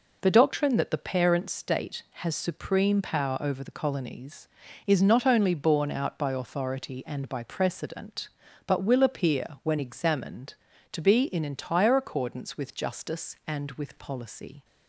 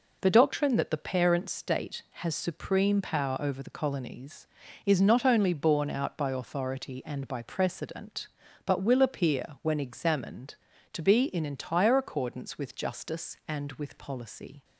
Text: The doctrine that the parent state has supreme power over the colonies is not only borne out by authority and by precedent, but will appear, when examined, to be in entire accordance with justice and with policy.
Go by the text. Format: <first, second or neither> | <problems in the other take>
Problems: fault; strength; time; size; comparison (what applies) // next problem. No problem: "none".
neither | none